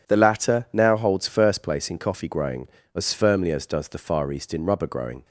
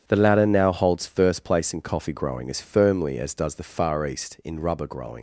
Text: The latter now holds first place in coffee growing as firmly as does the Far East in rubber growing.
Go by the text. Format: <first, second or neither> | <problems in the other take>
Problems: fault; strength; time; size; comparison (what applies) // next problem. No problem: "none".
first | starts louder than the rest; strong; until 1.1 s; 8.5 dB // leaves "growing" unfinished; at 5.1 s; 95 ms